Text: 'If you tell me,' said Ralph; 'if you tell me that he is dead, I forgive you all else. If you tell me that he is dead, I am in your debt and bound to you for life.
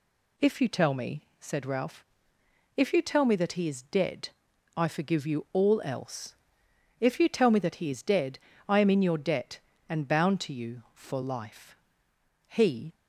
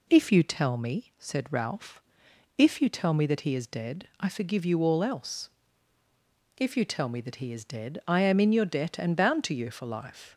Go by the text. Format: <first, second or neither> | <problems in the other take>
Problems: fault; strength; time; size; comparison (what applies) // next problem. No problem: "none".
second | goes on to say "He"; slight; from 12.4 s on; 0.46 s long